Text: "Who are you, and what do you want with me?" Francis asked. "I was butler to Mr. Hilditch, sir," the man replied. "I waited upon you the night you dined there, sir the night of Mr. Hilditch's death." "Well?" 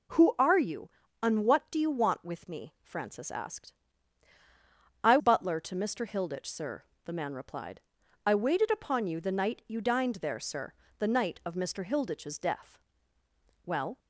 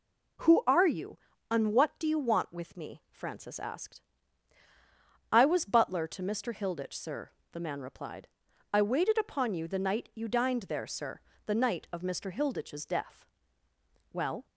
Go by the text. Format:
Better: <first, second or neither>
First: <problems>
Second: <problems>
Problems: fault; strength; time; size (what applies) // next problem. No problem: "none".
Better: second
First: skips "was"; at 5.1 s // pauses between "sir" and "the"; slight; at 10.7 s; 0.24 s long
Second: pauses between "sir" and "the"; slight; at 11.2 s; 0.24 s long